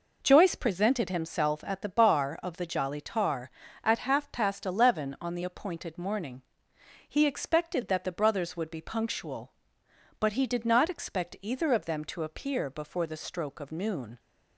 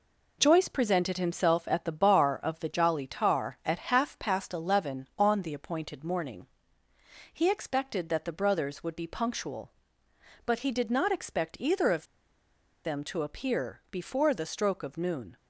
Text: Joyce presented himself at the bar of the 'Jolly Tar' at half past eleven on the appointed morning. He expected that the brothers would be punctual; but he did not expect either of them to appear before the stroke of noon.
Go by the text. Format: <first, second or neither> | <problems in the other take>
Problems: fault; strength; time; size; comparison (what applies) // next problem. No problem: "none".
first | pauses between "of" and "them"; noticeable; at 12.0 s; 0.79 s long